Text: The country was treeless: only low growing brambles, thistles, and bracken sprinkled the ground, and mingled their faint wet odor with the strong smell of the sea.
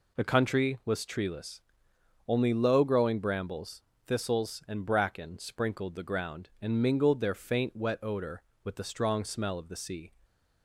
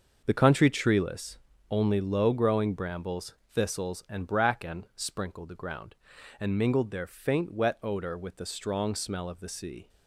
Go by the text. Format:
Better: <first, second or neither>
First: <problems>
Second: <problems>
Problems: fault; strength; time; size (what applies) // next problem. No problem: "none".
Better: first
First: none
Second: starts louder than the rest; until 1.2 s; 6 dB // skips "was"; at 0.6 s